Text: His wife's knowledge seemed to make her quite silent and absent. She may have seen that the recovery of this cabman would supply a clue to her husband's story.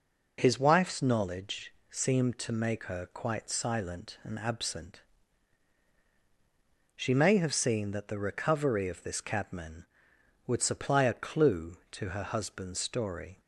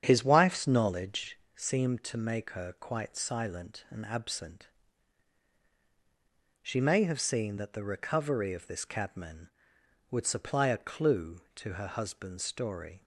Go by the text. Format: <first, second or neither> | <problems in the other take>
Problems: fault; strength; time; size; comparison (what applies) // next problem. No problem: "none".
first | starts louder than the rest; strong; until 1.5 s; 8.5 dB // pauses between "knowledge" and "seemed"; slight; at 1.3 s; 0.18 s long; slight in the first